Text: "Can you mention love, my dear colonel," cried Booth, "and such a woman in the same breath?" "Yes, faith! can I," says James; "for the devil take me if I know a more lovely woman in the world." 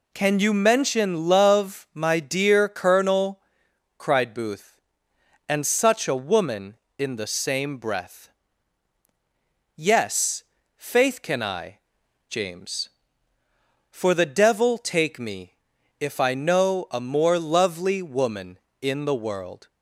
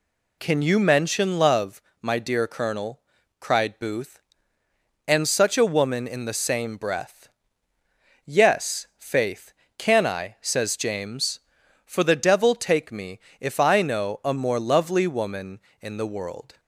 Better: second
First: skips "says"; at 12.0 s // pauses between "me" and "if"; at 15.5 s; 0.44 s long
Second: pauses between "me" and "if"; slight; at 13.1 s; 0.22 s long

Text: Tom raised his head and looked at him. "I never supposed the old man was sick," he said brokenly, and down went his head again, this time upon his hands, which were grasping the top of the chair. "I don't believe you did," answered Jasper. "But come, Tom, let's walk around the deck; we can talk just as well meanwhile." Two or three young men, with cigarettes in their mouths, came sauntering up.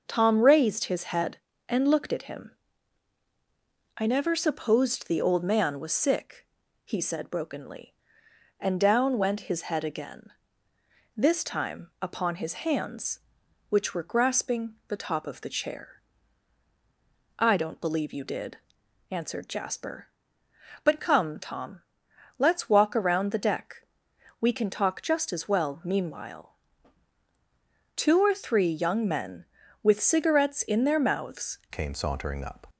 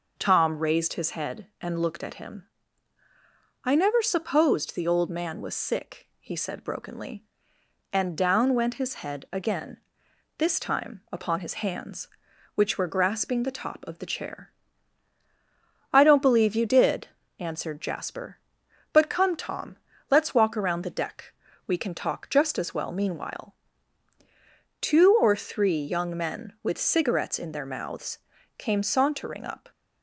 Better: second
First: starts louder than the rest; noticeable; until 1.0 s; 6 dB // changes voice at "came"; from 31.7 s on; 0.9 s long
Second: none

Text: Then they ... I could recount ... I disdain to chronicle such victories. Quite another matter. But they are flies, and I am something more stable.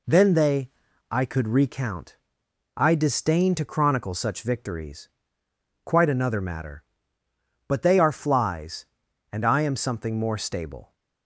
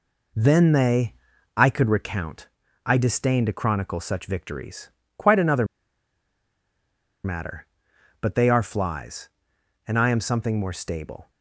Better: first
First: none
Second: pauses between "another" and "matter"; strong; at 5.6 s; 1.6 s long

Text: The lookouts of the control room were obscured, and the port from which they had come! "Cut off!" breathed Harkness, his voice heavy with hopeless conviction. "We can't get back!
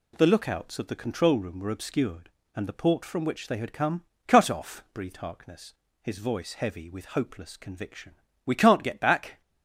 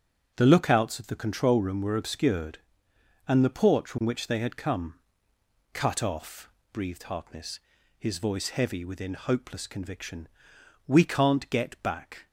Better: first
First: none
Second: starts louder than the rest; until 1.3 s; 7 dB // says "within" for "with"; at 8.8 s

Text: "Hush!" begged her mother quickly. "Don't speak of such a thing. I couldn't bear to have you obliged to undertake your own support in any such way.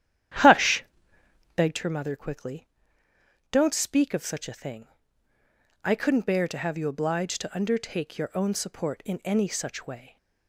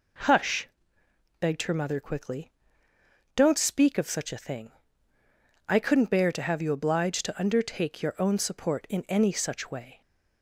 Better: second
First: starts louder than the rest; strong; until 1.8 s; 11 dB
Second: none

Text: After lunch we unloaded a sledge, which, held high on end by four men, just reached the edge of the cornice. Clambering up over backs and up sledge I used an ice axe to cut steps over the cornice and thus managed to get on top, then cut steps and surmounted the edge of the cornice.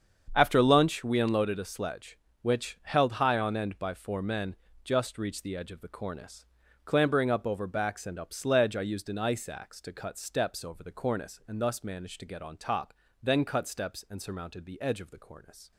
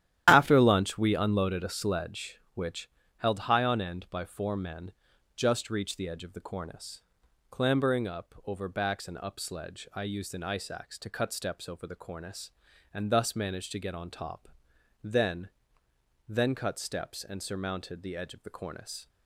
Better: first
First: starts louder than the rest; strong; until 1.3 s; 7.5 dB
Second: starts louder than the rest; strong; until 1.2 s; 11.5 dB // says "then" twice; at 16.3 s

